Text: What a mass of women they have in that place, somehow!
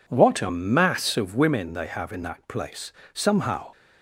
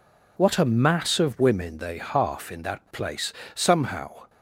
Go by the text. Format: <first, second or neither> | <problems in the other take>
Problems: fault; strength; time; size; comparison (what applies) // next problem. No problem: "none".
first | says "half" for "have"; at 1.9 s